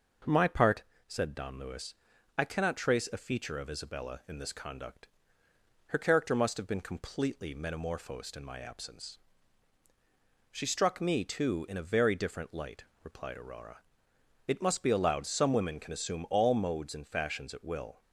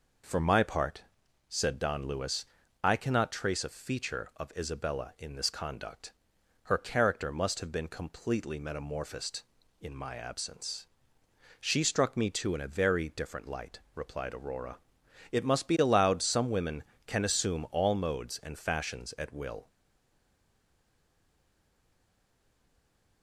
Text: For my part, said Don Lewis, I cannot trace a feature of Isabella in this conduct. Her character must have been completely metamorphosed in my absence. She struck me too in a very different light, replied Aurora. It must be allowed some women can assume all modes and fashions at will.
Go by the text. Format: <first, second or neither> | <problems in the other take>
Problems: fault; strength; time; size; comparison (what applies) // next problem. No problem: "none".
first | stays silent after the last word; strong; from 19.6 s on; 3.6 s long